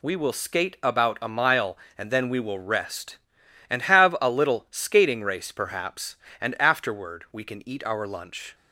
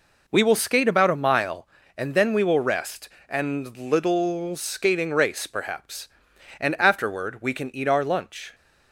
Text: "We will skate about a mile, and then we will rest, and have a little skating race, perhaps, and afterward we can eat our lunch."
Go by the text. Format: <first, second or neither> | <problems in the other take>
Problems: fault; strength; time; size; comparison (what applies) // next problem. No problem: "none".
first | skips "have a"; at 3.7 s